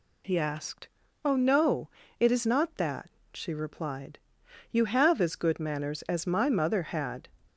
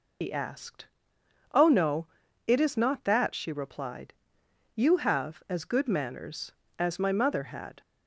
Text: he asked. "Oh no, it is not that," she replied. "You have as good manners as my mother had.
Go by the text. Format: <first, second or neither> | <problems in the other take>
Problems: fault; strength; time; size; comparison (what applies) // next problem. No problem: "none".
first | loses the start of "he"; at 0.2 s; 100 ms